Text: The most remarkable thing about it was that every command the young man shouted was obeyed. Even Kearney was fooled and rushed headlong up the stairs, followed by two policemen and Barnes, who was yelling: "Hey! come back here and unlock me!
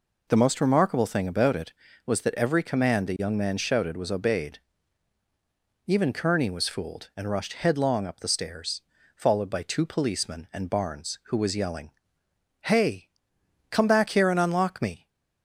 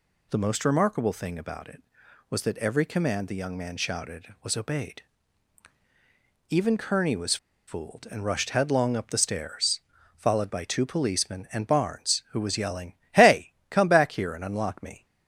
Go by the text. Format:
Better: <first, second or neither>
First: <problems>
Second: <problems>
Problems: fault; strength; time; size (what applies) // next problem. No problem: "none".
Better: first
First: none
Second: pauses between "was" and "fooled"; slight; at 7.3 s; 0.31 s long